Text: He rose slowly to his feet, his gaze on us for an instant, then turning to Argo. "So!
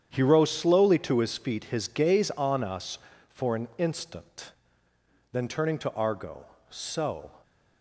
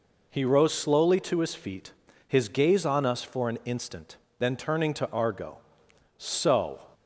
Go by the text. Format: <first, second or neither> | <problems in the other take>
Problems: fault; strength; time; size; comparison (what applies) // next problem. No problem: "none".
second | gets quieter; strong; throughout; 10.5 dB